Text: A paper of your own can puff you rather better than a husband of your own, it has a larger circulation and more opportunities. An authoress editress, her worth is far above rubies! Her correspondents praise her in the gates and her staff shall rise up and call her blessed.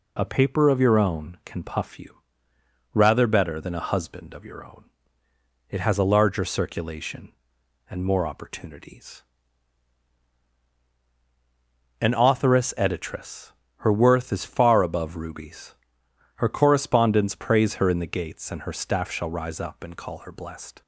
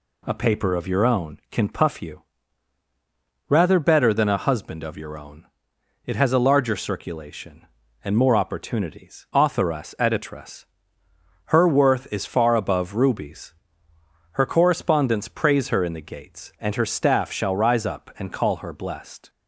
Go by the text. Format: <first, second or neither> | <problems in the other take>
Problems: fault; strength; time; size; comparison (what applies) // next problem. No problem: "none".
first | pauses between "you" and "rather"; strong; at 2.2 s; 1.2 s long; noticeable in the first // skips "An"; at 9.3 s